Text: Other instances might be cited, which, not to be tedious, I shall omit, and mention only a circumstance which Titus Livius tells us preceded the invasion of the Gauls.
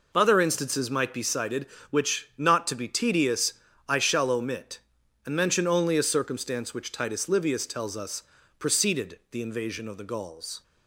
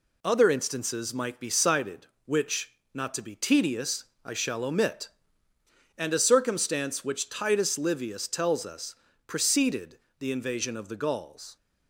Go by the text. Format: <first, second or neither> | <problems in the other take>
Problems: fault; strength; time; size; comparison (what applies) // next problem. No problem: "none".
first | skips "mention only"; at 6.1 s // pauses between "us" and "preceded"; slight; at 8.9 s; 0.32 s long; slight in the first // pauses between "preceded" and "the"; slight; at 9.9 s; 0.20 s long